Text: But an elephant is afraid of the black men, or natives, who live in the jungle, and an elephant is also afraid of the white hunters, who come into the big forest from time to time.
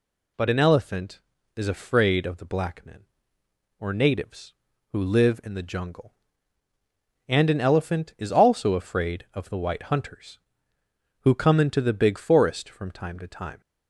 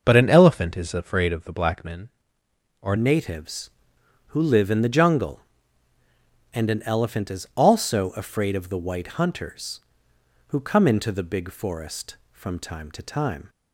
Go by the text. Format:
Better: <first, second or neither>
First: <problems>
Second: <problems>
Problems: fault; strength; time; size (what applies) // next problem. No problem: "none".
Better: first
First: none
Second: changes voice at "natives"; from 2.9 s on; 10.5 s long